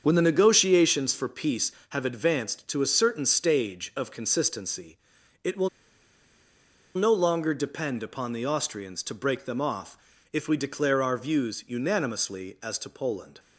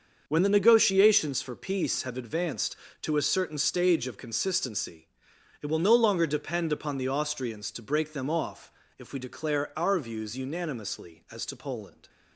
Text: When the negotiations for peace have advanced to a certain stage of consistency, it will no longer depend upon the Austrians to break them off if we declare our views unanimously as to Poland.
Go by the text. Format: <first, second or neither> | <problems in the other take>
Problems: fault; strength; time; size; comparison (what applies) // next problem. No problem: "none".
second | starts louder than the rest; until 1.0 s; 7 dB; also in the second // pauses between "will" and "no"; strong; at 5.6 s; 1.2 s long // pauses between "off" and "if"; slight; at 9.9 s; 0.36 s long; slight in the second